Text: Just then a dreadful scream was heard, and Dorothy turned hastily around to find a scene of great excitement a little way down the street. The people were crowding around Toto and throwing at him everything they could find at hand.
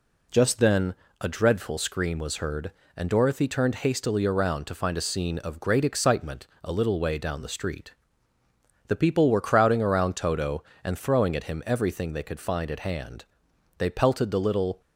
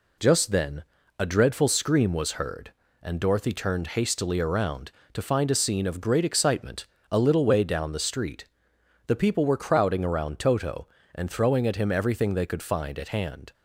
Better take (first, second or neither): second